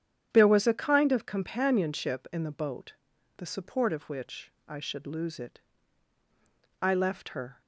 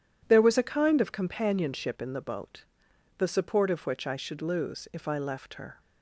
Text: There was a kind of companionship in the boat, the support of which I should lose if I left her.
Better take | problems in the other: second | starts louder than the rest; strong; until 1.3 s; 9 dB // pauses between "which" and "I"; slight; at 4.5 s; 0.16 s long // says "it" for "if"; at 5.4 s

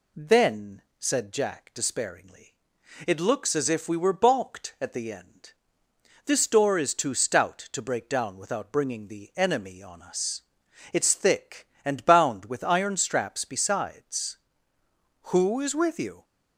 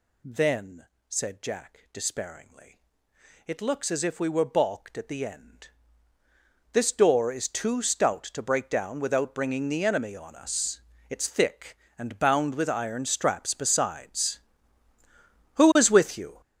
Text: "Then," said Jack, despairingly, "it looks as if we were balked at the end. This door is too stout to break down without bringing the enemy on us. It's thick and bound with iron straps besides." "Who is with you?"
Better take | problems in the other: first | gets louder; strong; throughout; 12 dB

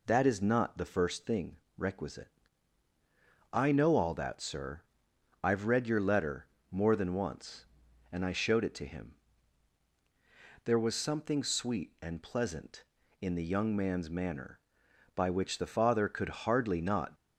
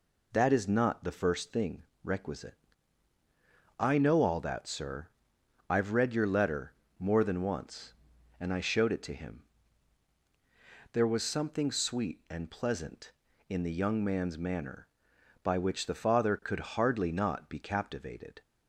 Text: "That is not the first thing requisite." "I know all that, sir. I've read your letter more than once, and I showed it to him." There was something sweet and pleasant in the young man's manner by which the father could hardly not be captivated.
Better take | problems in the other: second | pauses between "thing" and "requisite"; slight; at 1.5 s; 0.22 s long; slight in the second // pauses between "letter" and "more"; slight; at 6.4 s; 0.26 s long; slight in the second // stops before "be captivated"; at 17.1 s

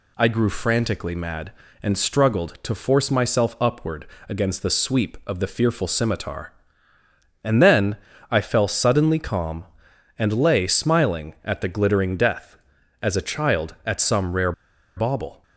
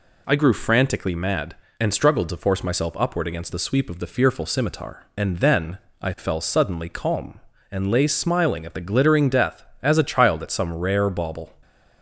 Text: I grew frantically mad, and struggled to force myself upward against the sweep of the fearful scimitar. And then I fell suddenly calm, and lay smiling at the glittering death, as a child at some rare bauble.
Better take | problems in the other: second | pauses between "upward" and "against"; slight; at 4.0 s; 0.22 s long // pauses between "then" and "I"; slight; at 7.9 s; 0.34 s long; slight in the second // pauses between "rare" and "bauble"; at 14.5 s; 0.44 s long

